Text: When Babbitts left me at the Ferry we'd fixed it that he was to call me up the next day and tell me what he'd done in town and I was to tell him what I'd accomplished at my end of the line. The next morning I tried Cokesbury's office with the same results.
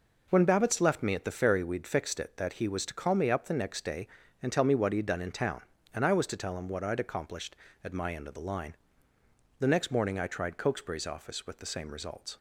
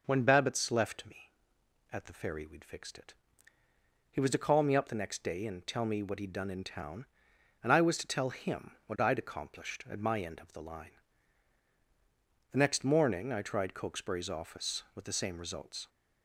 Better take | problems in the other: first | skips "that"; at 3.6 s

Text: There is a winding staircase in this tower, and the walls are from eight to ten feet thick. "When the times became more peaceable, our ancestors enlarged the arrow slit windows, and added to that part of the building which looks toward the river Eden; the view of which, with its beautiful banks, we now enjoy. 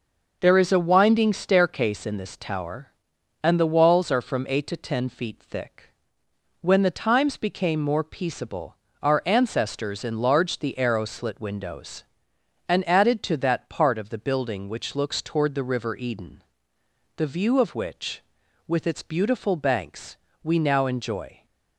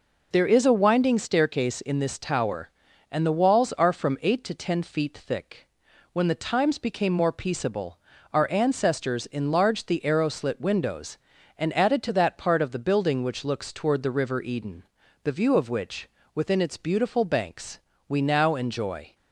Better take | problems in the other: first | says "within" for "with"; at 16.3 s

